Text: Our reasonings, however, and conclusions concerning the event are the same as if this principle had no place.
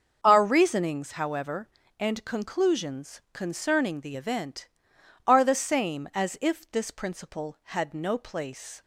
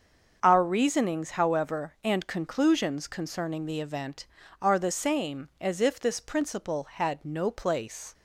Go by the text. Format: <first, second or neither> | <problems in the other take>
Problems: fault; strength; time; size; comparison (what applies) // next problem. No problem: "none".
neither | starts louder than the rest; the same in both